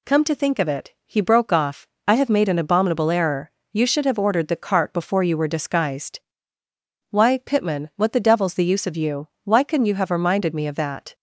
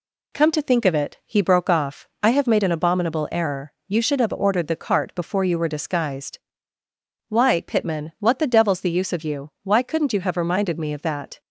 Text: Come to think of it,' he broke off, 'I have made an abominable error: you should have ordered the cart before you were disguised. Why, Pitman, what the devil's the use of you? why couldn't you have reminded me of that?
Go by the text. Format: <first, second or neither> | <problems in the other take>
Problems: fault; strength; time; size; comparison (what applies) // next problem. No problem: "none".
neither | none